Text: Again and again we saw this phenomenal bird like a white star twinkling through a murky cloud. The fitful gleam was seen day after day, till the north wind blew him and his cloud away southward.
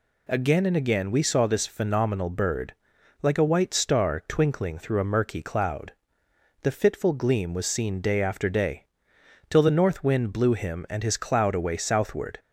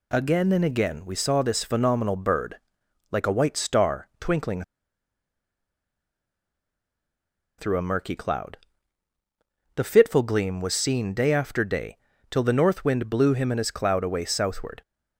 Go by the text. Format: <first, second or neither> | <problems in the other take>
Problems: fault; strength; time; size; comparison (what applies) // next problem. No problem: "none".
first | pauses between "bird" and "like"; noticeable; at 2.5 s; 0.54 s long; noticeable in the first // pauses between "twinkling" and "through"; strong; at 4.6 s; 2.9 s long